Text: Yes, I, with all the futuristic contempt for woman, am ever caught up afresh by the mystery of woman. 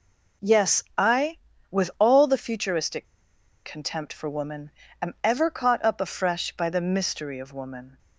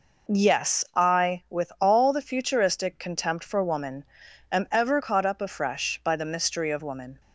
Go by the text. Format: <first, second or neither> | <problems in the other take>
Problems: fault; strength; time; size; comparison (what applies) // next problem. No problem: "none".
second | pauses between "futuristic" and "contempt"; noticeable; at 3.0 s; 0.59 s long